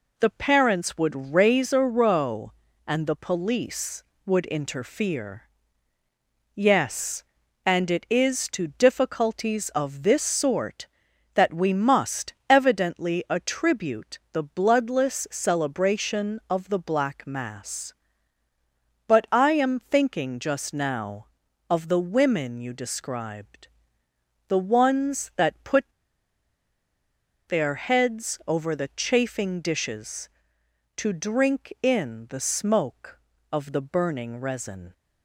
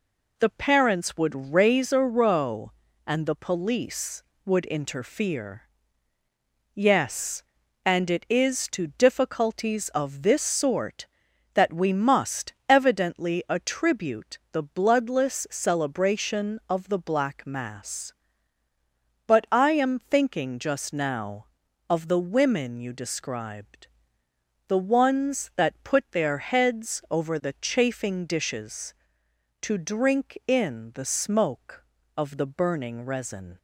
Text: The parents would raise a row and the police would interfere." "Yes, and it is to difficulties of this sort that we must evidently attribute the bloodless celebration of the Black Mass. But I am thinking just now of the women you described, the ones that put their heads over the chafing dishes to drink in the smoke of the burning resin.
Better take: second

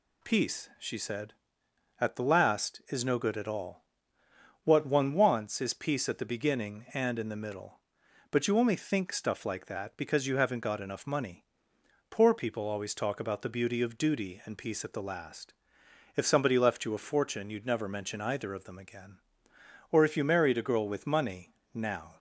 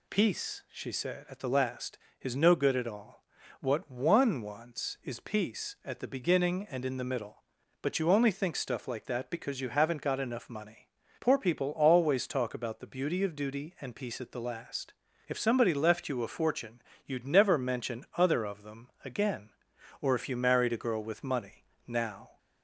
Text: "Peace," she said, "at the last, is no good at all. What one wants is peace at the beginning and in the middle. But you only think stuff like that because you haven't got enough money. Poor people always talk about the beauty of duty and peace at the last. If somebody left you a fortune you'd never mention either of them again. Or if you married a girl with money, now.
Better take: first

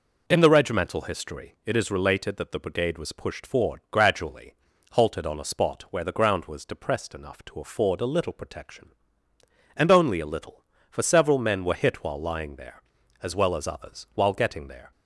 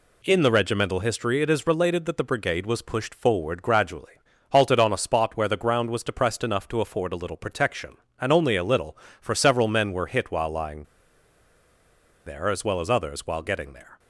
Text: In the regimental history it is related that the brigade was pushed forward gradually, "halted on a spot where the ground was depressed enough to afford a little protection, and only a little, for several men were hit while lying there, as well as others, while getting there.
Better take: first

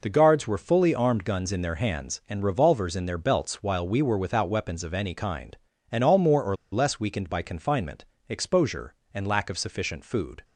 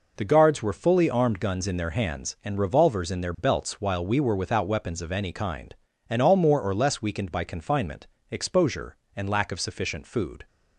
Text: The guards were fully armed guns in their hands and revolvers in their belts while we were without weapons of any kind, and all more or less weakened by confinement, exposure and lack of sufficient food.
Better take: second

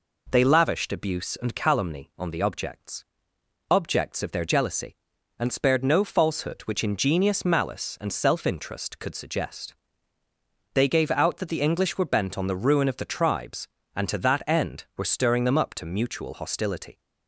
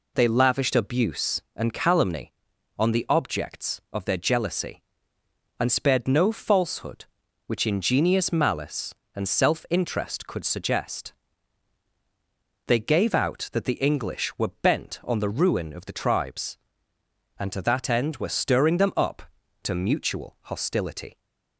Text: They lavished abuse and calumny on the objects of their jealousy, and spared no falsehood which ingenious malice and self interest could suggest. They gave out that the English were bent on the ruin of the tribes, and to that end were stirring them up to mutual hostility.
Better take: second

